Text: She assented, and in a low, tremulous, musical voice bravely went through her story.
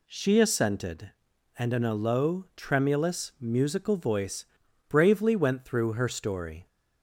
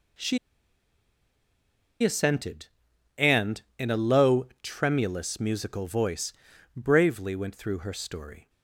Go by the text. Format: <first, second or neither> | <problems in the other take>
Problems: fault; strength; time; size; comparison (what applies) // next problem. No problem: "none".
first | pauses between "She" and "assented"; strong; at 0.3 s; 1.6 s long // pauses between "voice" and "bravely"; at 6.3 s; 0.42 s long; also in the first